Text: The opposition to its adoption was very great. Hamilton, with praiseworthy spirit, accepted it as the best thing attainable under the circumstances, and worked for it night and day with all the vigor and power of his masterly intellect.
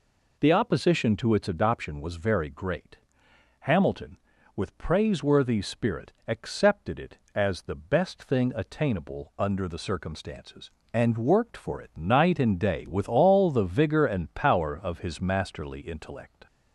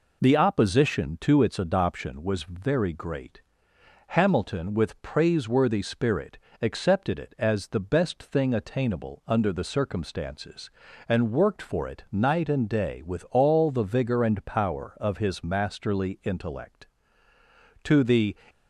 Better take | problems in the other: first | goes on to say "To the"; from 17.8 s on; 0.52 s long

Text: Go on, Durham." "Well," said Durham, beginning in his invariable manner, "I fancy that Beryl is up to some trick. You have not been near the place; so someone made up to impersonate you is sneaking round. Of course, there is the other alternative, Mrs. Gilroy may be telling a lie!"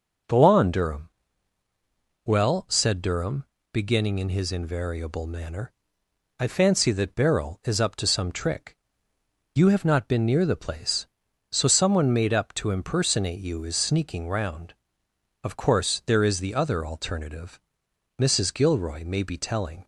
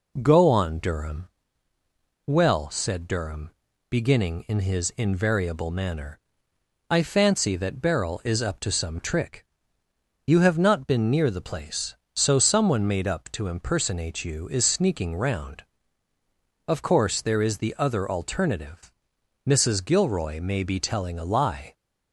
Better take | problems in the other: second | stops before "a lie"; at 19.8 s

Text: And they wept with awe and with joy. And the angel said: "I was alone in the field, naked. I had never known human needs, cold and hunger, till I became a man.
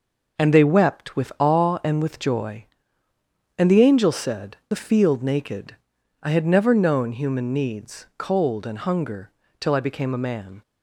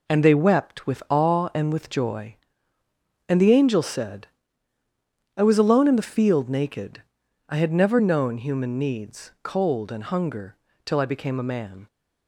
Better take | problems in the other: second | skips "I was alone in"; at 4.6 s

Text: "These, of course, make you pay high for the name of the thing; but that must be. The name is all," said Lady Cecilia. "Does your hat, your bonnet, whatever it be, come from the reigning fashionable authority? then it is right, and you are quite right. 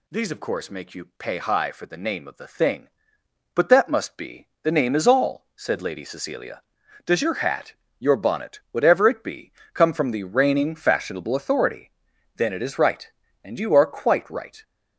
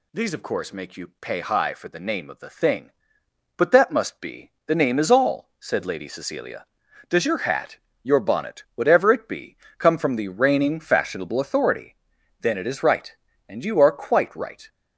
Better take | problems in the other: neither | none

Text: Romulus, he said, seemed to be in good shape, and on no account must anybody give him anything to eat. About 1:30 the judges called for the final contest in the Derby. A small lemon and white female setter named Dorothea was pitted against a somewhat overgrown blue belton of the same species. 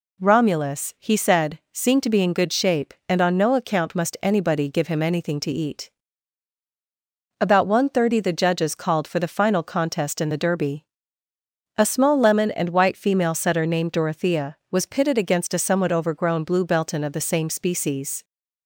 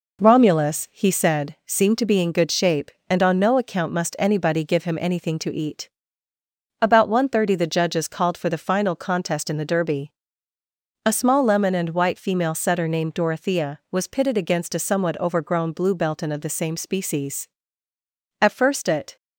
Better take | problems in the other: first | goes on to say "At first it"; noticeable; from 18.4 s on; 0.74 s long

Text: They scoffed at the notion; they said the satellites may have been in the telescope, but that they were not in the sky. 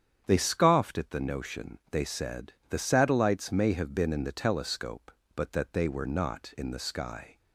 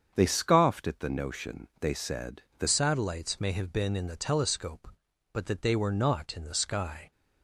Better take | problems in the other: first | starts louder than the rest; strong; until 1.1 s; 7.5 dB; strong in the first // pauses between "said" and "the"; slight; at 2.4 s; 0.16 s long; slight in the first // changes voice at "satellites"; from 2.6 s on; 4.5 s long

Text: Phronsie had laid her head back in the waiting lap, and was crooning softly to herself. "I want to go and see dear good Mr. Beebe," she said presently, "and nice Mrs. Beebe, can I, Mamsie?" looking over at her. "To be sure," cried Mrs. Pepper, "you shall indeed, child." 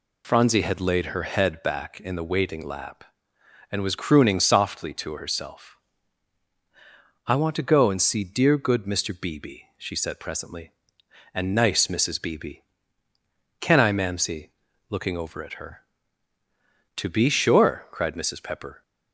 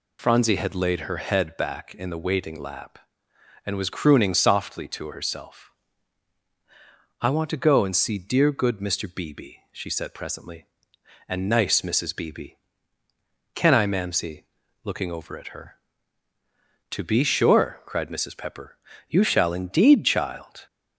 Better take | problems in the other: second | stops before "you shall indeed child"; at 18.8 s

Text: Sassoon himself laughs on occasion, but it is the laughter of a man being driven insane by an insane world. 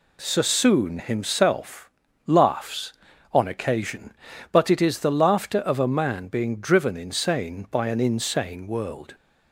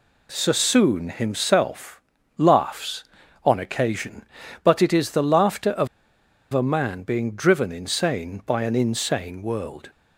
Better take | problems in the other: first | pauses between "himself" and "laughs"; at 2.0 s; 0.38 s long; also in the first // pauses between "of" and "a"; noticeable; at 5.8 s; 0.66 s long

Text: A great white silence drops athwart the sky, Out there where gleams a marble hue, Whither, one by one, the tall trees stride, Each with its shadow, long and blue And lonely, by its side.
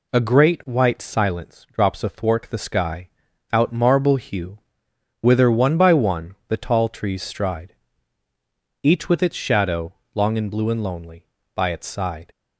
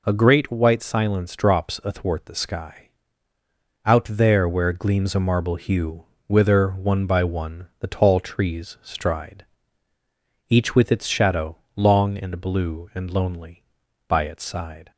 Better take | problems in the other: second | skips "there where gleams a"; at 3.7 s

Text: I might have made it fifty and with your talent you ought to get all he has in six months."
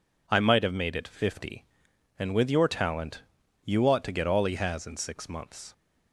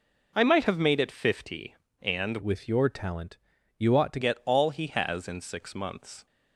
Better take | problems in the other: first | changes voice from "with" to "to"; from 2.3 to 4.1 s; 1.8 s long // pauses between "talent" and "you"; at 3.3 s; 0.42 s long; also in the first

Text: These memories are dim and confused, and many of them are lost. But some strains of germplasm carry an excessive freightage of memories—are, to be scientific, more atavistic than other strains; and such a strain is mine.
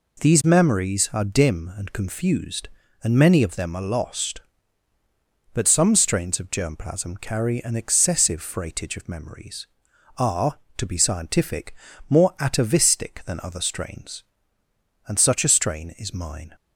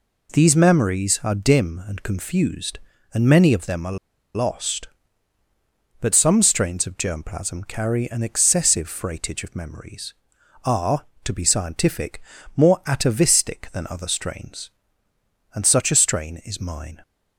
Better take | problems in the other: first | pauses between "are" and "lost"; at 3.9 s; 0.39 s long

